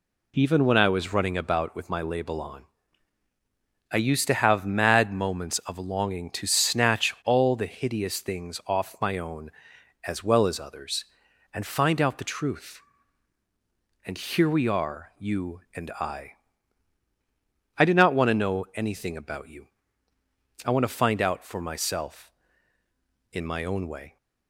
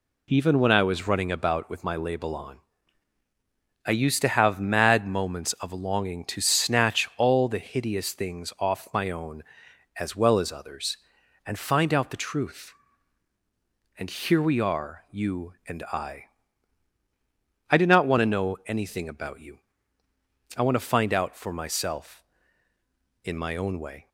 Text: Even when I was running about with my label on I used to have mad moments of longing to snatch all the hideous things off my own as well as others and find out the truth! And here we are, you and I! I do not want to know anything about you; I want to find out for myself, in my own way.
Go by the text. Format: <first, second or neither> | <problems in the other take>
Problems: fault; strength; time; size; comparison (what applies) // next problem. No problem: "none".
neither | pauses between "on" and "I"; the same in both